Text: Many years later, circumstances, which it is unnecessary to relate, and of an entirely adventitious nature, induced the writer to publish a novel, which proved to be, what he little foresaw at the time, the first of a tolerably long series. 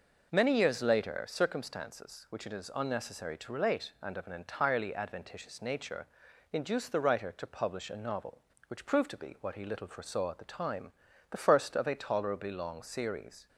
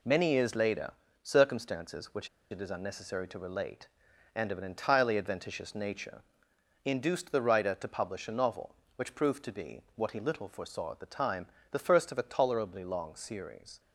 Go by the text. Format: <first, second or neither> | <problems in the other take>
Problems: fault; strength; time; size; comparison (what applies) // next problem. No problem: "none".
first | pauses between "which" and "it"; slight; at 2.2 s; 0.23 s long